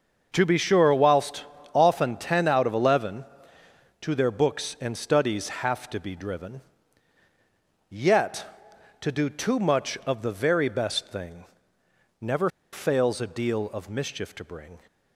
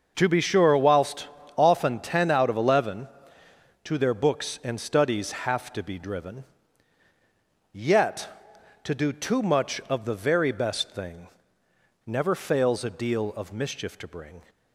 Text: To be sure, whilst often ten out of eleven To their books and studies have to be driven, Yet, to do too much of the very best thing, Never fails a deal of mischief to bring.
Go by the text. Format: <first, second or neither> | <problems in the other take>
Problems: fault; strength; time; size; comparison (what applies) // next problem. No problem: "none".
second | starts louder than the rest; until 1.3 s; 6.5 dB; also in the second // pauses between "whilst" and "often"; slight; at 1.4 s; 0.30 s long; slight in the second // pauses between "Never" and "fails"; slight; at 12.4 s; 0.24 s long